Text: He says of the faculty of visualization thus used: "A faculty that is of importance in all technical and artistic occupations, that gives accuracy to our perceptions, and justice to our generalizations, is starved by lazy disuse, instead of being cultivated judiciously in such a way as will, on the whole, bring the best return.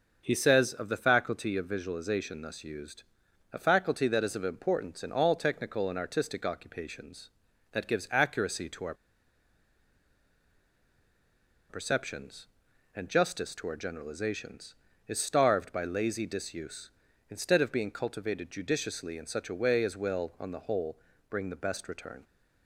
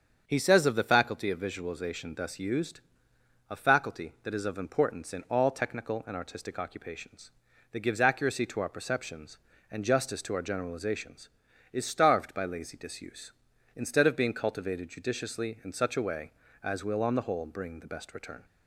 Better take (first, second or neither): second